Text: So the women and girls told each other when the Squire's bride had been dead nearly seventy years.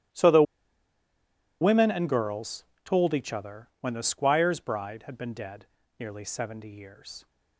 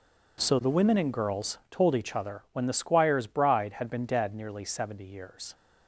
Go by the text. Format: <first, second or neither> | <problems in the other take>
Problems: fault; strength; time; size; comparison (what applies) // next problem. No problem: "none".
second | starts louder than the rest; strong; until 2.3 s; 14.5 dB // pauses between "the" and "women"; at 0.4 s; 1.1 s long // pauses between "girls" and "told"; slight; at 2.6 s; 0.20 s long // pauses between "dead" and "nearly"; slight; at 5.6 s; 0.32 s long